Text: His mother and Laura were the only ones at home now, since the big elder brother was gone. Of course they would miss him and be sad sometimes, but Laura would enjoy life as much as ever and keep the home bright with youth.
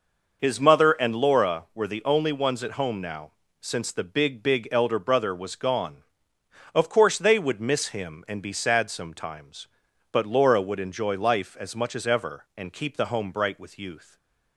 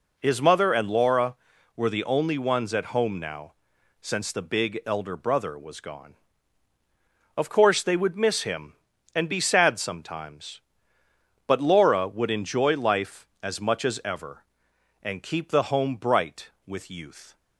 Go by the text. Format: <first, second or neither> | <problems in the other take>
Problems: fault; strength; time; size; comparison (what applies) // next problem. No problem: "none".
second | says "big" twice; at 4.4 s // stays silent after the last word; slight; from 14.0 s on; 0.5 s long